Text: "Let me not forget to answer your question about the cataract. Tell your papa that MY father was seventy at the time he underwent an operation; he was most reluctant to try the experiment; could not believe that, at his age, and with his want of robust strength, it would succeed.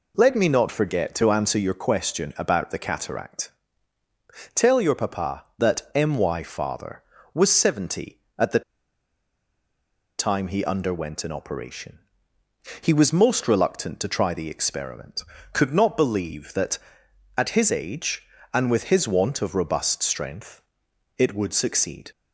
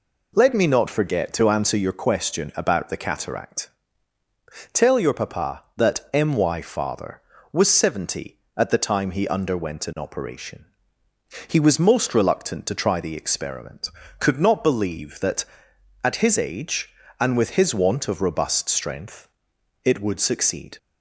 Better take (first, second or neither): second